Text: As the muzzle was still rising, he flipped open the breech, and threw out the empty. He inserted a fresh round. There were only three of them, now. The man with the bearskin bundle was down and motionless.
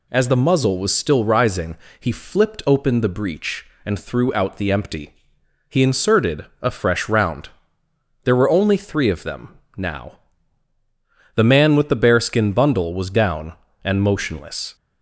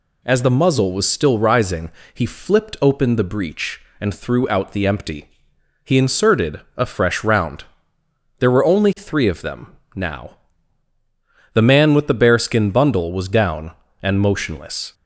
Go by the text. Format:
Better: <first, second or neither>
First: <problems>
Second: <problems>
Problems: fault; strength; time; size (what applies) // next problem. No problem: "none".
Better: neither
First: none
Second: none